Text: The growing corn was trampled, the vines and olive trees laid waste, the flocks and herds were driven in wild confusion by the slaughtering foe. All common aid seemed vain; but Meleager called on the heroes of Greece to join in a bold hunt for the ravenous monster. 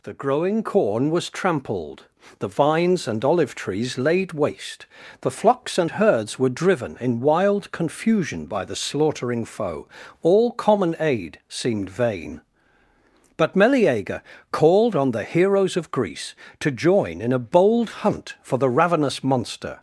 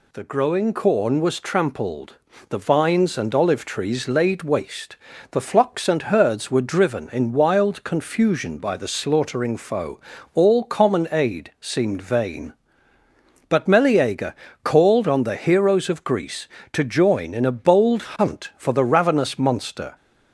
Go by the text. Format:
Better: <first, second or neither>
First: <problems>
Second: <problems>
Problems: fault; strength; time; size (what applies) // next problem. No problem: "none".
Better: neither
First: pauses between "Meleager" and "called"; slight; at 14.2 s; 0.30 s long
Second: pauses between "Meleager" and "called"; slight; at 14.3 s; 0.30 s long